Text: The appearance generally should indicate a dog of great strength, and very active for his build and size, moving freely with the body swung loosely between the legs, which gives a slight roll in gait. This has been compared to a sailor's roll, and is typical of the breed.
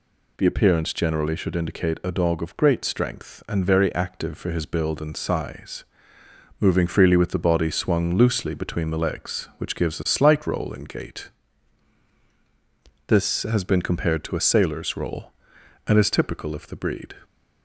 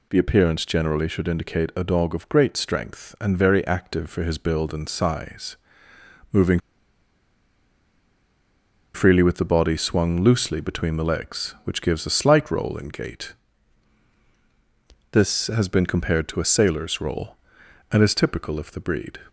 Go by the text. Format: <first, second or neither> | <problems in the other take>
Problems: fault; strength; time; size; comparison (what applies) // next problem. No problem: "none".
first | pauses between "moving" and "freely"; strong; at 6.6 s; 2.3 s long